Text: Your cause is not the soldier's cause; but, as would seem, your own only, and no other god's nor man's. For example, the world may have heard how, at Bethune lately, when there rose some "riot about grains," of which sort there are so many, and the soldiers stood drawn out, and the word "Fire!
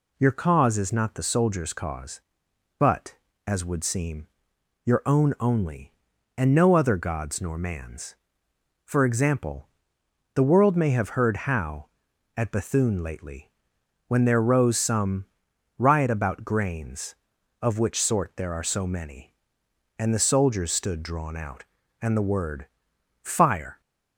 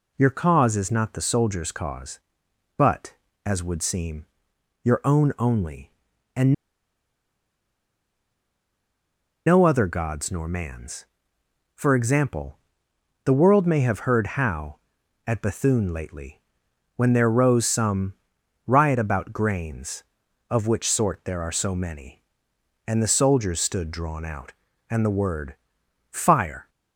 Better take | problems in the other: first | pauses between "and" and "no"; strong; at 6.5 s; 2.9 s long // pauses between "some" and "riot"; noticeable; at 18.1 s; 0.50 s long; noticeable in the first // pauses between "word" and "Fire"; noticeable; at 25.5 s; 0.54 s long; noticeable in the first

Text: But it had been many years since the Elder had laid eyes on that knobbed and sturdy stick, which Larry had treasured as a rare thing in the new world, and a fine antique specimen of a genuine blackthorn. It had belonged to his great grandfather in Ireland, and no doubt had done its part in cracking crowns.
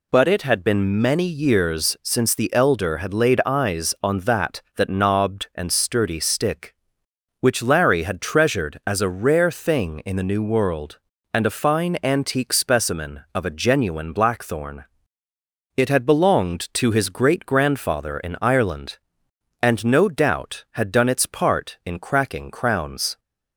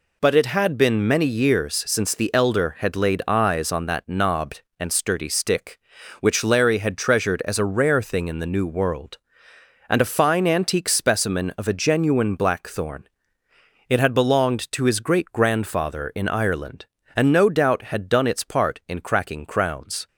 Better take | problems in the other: second | says "that" twice; at 4.7 s

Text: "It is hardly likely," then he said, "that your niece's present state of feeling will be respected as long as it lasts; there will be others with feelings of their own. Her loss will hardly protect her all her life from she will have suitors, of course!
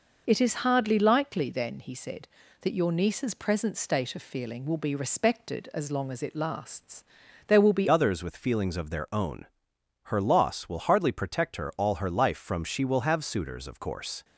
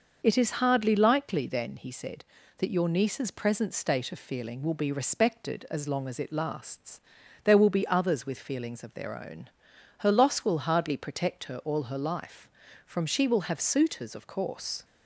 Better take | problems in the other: second | changes voice at "others"; from 7.8 s on; 6.4 s long

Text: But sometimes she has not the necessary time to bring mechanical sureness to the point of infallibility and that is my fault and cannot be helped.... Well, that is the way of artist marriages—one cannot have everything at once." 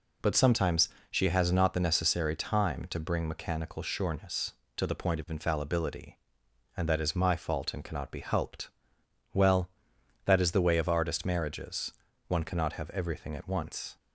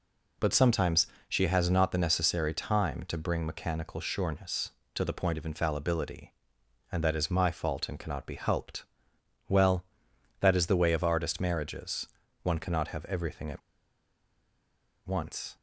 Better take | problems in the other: first | pauses between "sometimes" and "she"; slight; at 1.0 s; 0.20 s long; slight in the first // pauses between "at" and "once"; strong; at 13.6 s; 1.4 s long

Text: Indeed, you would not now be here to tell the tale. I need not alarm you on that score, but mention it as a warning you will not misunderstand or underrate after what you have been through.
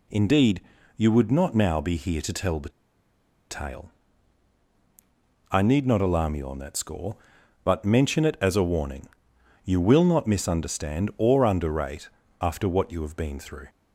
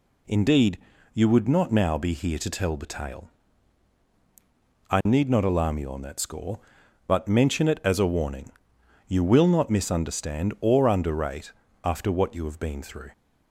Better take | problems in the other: second | pauses between "the" and "tale"; noticeable; at 2.6 s; 0.80 s long // pauses between "warning" and "you"; noticeable; at 9.0 s; 0.58 s long; noticeable in the second // pauses between "underrate" and "after"; slight; at 12.0 s; 0.32 s long; slight in the second

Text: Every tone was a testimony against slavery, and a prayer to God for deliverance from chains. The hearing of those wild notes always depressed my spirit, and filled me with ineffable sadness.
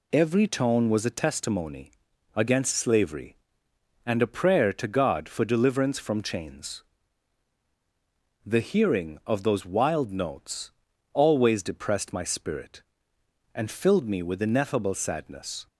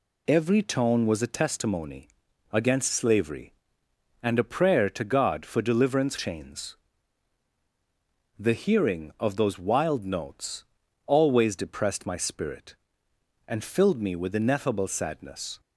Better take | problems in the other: first | pauses between "testimony" and "against"; at 2.0 s; 0.42 s long; also in the first // skips "from"; at 6.1 s // pauses between "notes" and "always"; at 10.6 s; 0.42 s long; also in the first

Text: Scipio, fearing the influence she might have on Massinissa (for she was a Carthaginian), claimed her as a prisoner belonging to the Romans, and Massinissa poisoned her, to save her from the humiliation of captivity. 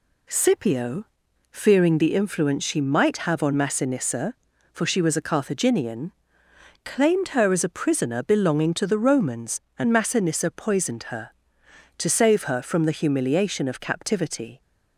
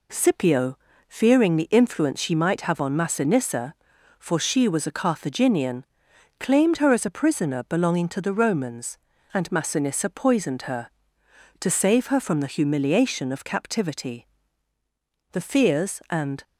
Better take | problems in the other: first | goes on to say "The fears and"; noticeable; from 15.3 s on; 1.1 s long

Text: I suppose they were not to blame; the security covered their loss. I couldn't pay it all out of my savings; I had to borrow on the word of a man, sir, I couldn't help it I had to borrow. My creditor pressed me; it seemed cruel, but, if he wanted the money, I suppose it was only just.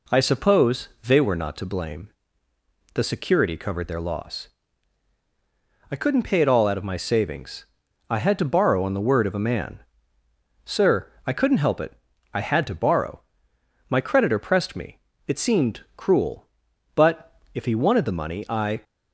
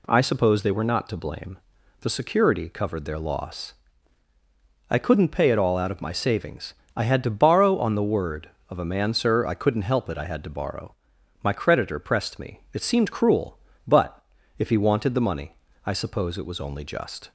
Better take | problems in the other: second | pauses between "suppose" and "they"; slight; at 0.8 s; 0.18 s long // pauses between "it" and "I"; at 11.9 s; 0.42 s long // stops before "suppose it was only just"; at 18.8 s

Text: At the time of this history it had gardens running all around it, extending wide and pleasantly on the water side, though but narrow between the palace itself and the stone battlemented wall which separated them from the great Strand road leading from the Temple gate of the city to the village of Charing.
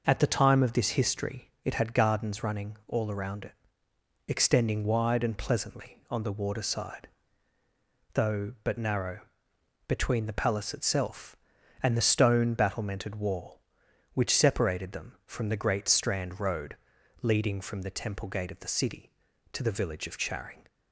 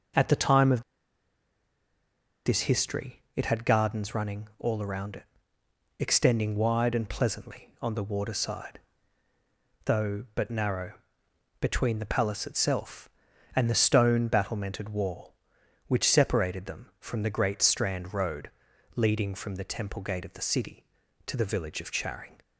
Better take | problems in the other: first | pauses between "of" and "this"; strong; at 0.8 s; 1.6 s long // pauses between "narrow" and "between"; noticeable; at 10.9 s; 0.68 s long; noticeable in the first // pauses between "road" and "leading"; noticeable; at 18.4 s; 0.46 s long; noticeable in the first

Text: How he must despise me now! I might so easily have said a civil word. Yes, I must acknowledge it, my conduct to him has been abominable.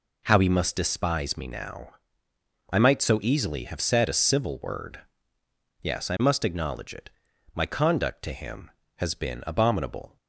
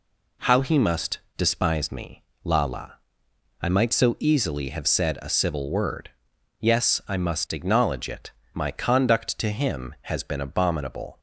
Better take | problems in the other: first | pauses between "must" and "despise"; slight; at 1.1 s; 0.18 s long // says "lala" for "now"; at 2.4 s

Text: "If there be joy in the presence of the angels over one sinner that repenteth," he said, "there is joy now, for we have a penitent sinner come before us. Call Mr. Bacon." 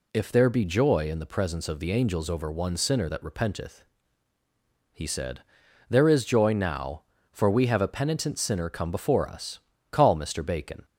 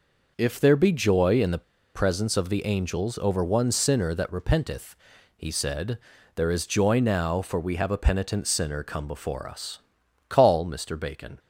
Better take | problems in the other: first | pauses between "the" and "presence"; slight; at 1.6 s; 0.33 s long

